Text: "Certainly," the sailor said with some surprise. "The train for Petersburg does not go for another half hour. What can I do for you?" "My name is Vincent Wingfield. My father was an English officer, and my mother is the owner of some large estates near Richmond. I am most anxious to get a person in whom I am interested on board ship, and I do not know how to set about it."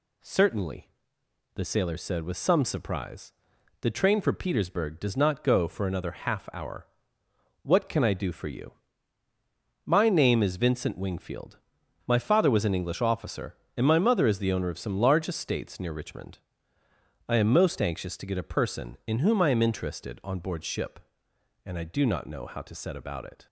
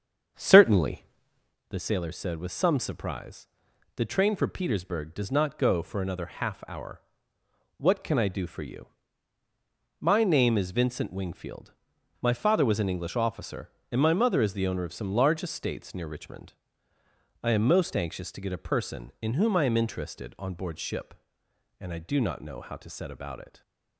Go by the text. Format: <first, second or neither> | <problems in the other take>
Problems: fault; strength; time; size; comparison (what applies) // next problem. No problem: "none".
first | starts louder than the rest; strong; until 1.6 s; 7 dB // stays silent after the last word; slight; from 23.4 s on; 0.5 s long